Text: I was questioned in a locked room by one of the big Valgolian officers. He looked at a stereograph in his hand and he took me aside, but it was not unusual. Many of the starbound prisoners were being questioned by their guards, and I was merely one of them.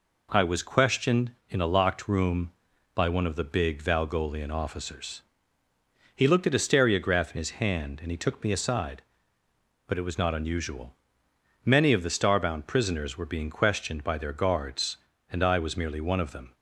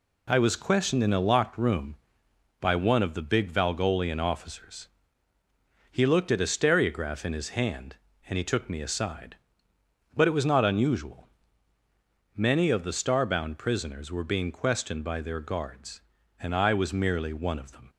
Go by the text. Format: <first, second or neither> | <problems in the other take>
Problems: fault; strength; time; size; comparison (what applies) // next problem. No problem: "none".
neither | none